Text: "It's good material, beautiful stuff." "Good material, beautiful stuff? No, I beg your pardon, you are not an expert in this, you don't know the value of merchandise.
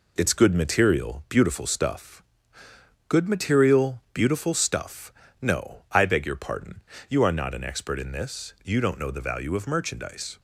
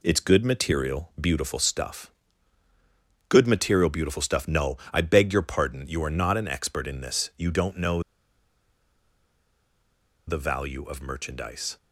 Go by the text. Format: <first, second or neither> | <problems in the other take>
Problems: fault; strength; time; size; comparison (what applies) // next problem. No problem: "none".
first | pauses between "know" and "the"; strong; at 8.0 s; 2.2 s long